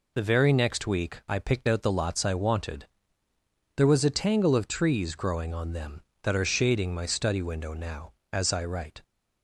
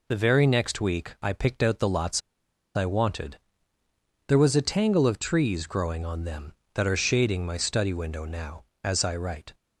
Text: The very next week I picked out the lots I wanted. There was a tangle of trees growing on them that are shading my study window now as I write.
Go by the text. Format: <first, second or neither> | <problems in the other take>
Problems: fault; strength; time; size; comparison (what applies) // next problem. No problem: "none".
first | pauses between "lots" and "I"; noticeable; at 2.2 s; 0.55 s long